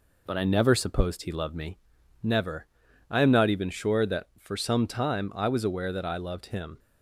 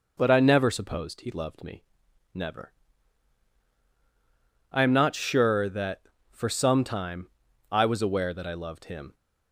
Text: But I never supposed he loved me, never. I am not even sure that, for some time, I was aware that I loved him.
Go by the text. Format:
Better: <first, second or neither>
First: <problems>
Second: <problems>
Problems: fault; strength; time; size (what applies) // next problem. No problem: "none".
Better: first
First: none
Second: skips "even"; at 5.1 s